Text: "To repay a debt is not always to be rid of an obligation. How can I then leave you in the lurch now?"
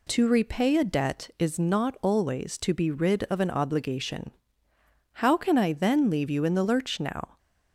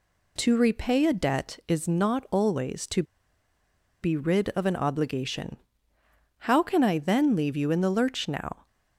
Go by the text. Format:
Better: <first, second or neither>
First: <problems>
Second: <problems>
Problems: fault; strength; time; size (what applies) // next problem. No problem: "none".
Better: first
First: none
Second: pauses between "to" and "be"; at 3.0 s; 1.0 s long